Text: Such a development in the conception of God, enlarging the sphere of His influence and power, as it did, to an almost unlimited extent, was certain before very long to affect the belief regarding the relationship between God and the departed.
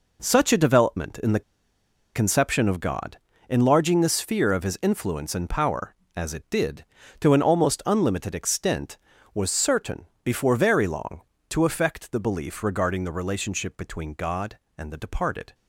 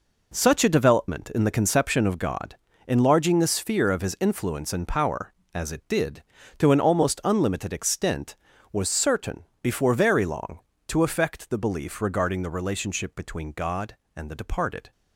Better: second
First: pauses between "the" and "conception"; noticeable; at 1.4 s; 0.74 s long // pauses between "certain" and "before"; slight; at 10.0 s; 0.18 s long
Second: pauses between "certain" and "before"; slight; at 9.4 s; 0.18 s long

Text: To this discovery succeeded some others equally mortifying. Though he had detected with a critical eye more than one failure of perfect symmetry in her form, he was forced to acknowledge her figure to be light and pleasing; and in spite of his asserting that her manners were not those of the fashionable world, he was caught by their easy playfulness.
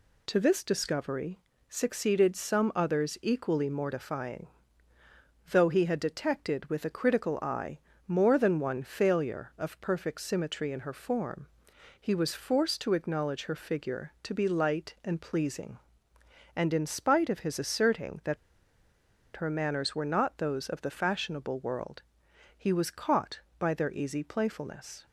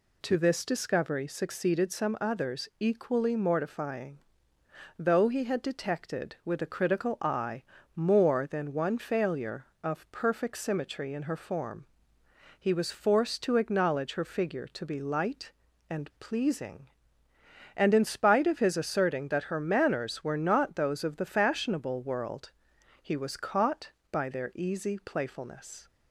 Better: second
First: pauses between "discovery" and "succeeded"; slight; at 1.3 s; 0.30 s long // pauses between "eye" and "more"; slight; at 7.7 s; 0.28 s long // pauses between "that" and "her"; at 18.3 s; 1.0 s long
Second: pauses between "eye" and "more"; slight; at 7.6 s; 0.32 s long

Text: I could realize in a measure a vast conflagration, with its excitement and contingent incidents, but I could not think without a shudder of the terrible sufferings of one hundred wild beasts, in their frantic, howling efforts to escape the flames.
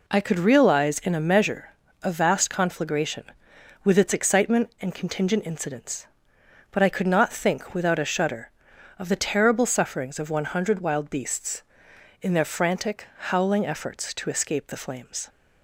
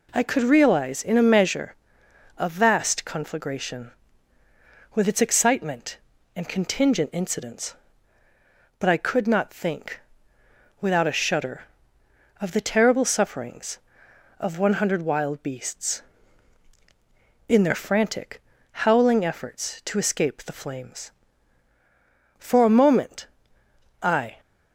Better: first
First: pauses between "measure" and "a"; slight; at 1.7 s; 0.28 s long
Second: pauses between "measure" and "a"; noticeable; at 1.7 s; 0.60 s long // pauses between "think" and "without"; noticeable; at 9.9 s; 0.80 s long // goes on to say "For a moment I"; strong; from 22.4 s on; 1.9 s long

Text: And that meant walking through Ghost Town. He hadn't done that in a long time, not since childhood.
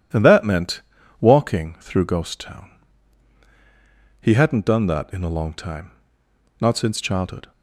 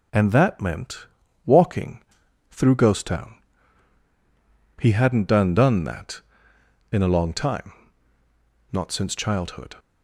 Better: first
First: pauses between "meant" and "walking"; at 0.8 s; 0.40 s long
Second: pauses between "meant" and "walking"; at 1.0 s; 0.38 s long // pauses between "walking" and "through"; noticeable; at 2.0 s; 0.48 s long // says "done" twice; at 5.5 s

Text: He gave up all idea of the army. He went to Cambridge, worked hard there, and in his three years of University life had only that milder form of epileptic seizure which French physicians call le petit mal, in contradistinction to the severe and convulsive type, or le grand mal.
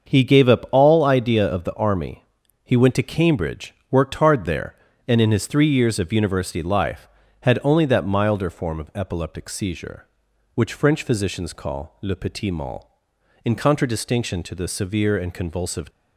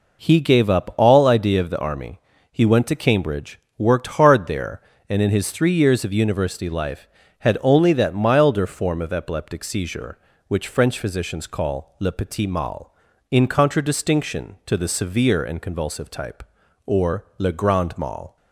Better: second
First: starts louder than the rest; until 1.1 s; 6.5 dB // stops before "type or le grand mal"; at 15.9 s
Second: none

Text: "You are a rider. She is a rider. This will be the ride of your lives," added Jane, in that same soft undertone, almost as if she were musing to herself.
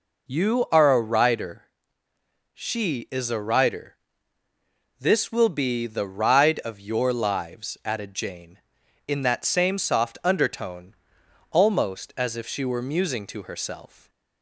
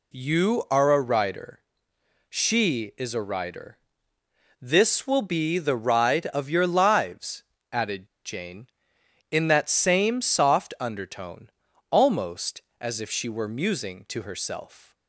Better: first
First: none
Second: pauses between "added" and "Jane"; slight; at 8.0 s; 0.17 s long

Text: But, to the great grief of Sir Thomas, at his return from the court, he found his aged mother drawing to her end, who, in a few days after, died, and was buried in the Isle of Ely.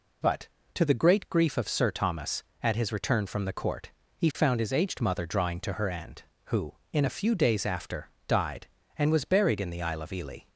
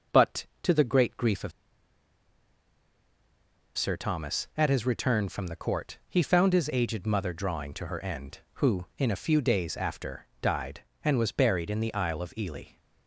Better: first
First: none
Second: pauses between "of" and "Sir"; strong; at 1.5 s; 2.2 s long

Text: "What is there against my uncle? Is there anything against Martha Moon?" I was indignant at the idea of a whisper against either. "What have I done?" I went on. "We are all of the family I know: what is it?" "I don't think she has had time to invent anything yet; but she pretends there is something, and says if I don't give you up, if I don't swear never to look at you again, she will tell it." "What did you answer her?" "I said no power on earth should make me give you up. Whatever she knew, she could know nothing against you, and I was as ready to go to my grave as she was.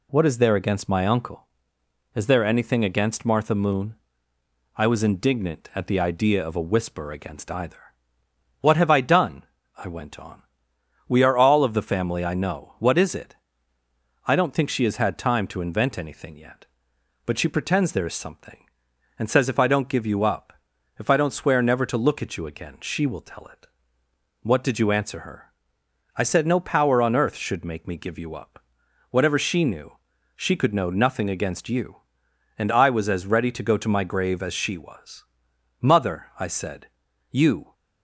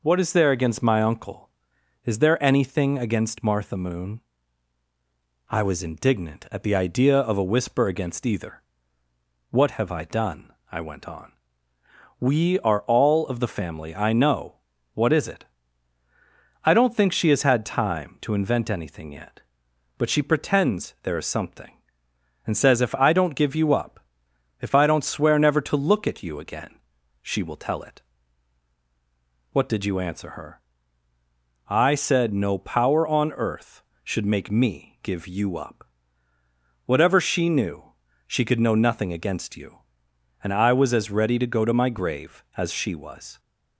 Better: second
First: goes on to say "Mother I said you"; strong; from 35.8 s on; 1.9 s long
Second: none

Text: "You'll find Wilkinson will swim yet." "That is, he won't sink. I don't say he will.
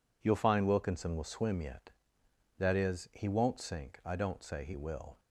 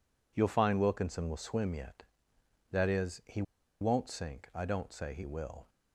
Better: first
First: none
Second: pauses between "he" and "won't"; at 3.4 s; 0.38 s long

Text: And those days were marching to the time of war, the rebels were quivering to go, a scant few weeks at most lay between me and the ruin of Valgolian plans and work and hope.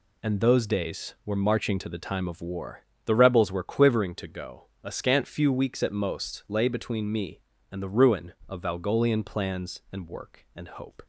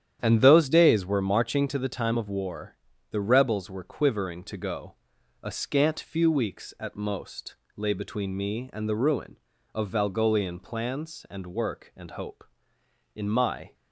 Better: first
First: none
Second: starts louder than the rest; strong; until 1.2 s; 9.5 dB // pauses between "most" and "lay"; slight; at 7.5 s; 0.20 s long // goes on to say "In my"; from 13.1 s on; 0.58 s long

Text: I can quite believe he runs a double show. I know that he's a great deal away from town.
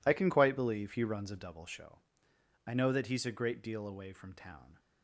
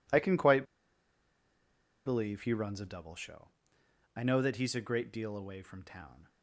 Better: first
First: none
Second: pauses between "quite" and "believe"; strong; at 0.6 s; 1.4 s long

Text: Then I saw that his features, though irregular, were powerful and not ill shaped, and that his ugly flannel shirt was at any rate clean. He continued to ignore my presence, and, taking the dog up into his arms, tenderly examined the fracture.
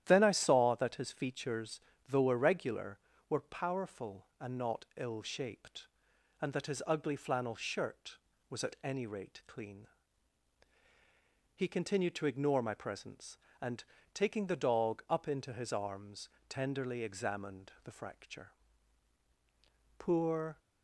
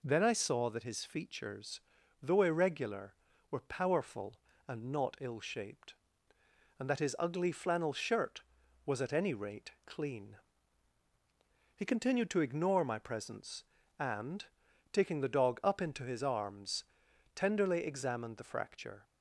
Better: second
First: starts louder than the rest; strong; until 1.0 s; 11.5 dB // goes on to say "Poor"; noticeable; from 19.9 s on; 0.62 s long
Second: none

